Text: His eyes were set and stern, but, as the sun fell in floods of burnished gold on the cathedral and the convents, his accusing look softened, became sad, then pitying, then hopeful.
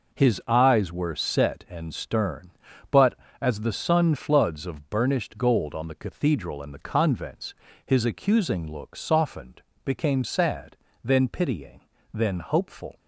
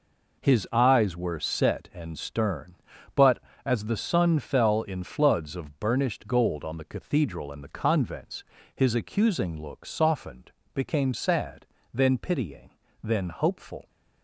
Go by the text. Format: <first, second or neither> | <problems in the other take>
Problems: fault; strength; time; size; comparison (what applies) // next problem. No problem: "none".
second | skips "fell in"; at 4.1 s